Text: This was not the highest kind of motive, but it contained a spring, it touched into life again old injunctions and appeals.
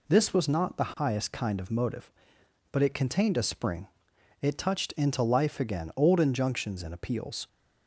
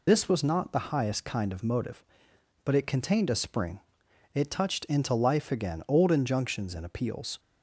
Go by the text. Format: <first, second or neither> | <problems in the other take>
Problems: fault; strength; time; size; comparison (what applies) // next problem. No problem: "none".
first | loses the start of "This"; at 0.0 s; 55 ms